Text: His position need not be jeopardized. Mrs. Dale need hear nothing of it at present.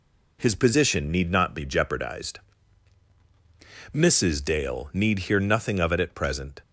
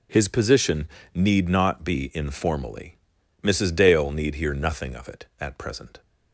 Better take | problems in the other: first | pauses between "position" and "need"; slight; at 0.8 s; 0.26 s long // says "informally" for "jeopardized"; at 2.1 s

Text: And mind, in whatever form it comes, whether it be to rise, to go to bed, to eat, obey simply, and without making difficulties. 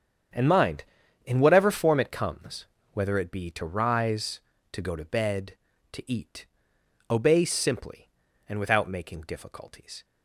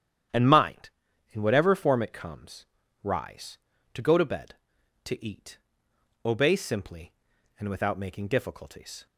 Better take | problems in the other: first | starts louder than the rest; strong; until 1.7 s; 9.5 dB; strong in the first // skips "whether it be to"; at 2.8 s

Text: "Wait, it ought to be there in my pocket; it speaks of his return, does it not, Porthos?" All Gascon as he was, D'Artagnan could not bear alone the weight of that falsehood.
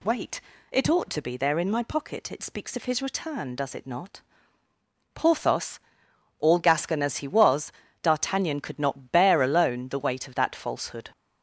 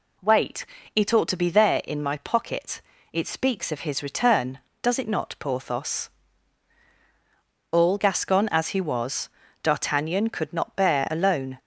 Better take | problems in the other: first | stops before "the weight of that falsehood"; at 11.5 s

